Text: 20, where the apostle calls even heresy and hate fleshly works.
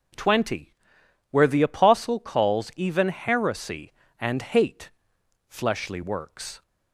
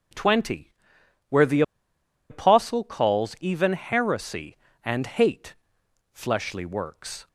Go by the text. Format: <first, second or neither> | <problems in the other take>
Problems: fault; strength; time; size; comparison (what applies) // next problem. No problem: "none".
first | pauses between "the" and "apostle"; noticeable; at 1.6 s; 0.67 s long // pauses between "hate" and "fleshly"; noticeable; at 5.5 s; 0.58 s long; noticeable in the first